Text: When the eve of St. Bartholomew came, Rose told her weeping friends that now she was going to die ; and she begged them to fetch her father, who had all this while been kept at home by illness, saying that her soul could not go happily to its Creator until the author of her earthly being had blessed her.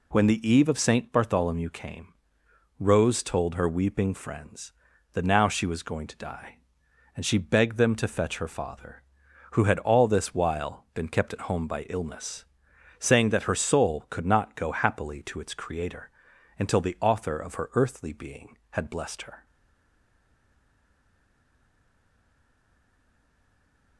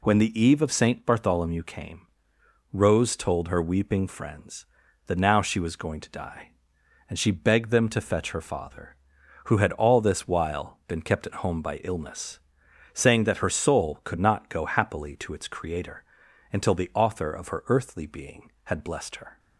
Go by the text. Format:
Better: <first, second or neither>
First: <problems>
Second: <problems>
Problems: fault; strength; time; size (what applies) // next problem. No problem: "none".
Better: second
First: pauses between "Creator" and "until"; noticeable; at 16.0 s; 0.48 s long // stays silent after the last word; strong; from 19.4 s on; 4.5 s long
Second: pauses between "Creator" and "until"; noticeable; at 16.0 s; 0.48 s long